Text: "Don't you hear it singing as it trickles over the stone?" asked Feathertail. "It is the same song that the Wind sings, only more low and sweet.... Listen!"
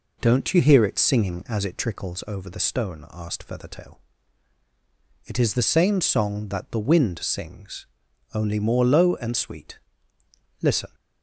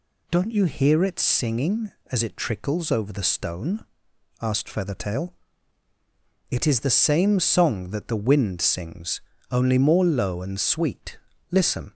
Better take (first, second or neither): second